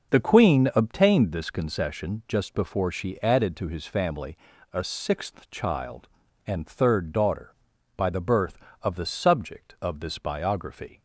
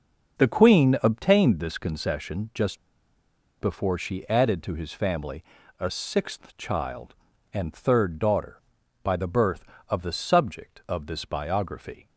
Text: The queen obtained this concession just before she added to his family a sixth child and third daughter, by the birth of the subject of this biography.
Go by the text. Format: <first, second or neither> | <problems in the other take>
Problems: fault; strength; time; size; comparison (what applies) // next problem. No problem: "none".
first | pauses between "just" and "before"; noticeable; at 2.7 s; 0.81 s long // pauses between "family" and "a"; at 5.4 s; 0.38 s long; also in the first